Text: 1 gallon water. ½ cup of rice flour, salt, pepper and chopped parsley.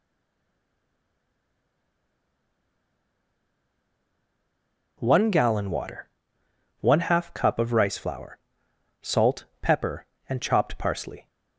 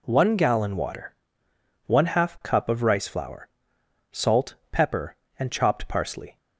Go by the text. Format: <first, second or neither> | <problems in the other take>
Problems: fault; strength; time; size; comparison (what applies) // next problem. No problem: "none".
second | stays silent before the first word; strong; until 4.9 s; 4.9 s long